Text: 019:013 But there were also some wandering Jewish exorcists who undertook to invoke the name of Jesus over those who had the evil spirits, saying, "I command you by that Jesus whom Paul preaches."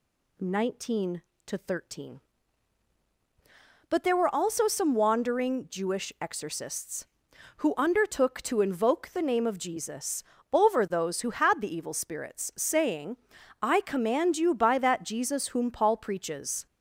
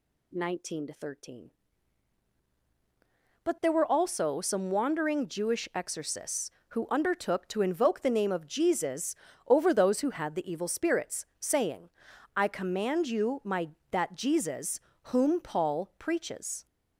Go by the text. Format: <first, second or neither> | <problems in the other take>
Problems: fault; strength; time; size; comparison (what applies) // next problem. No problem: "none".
first | pauses between "Jesus" and "over"; slight; at 9.1 s; 0.32 s long; slight in the first // says "my" for "by"; at 13.4 s // pauses between "Jesus" and "whom"; slight; at 14.8 s; 0.22 s long